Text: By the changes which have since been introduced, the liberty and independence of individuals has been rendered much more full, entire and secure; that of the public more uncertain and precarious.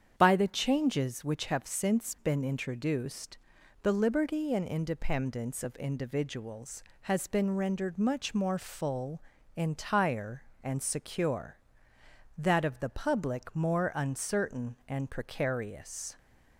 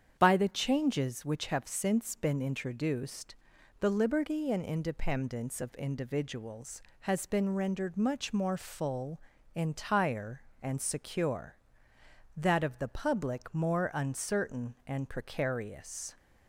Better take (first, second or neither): neither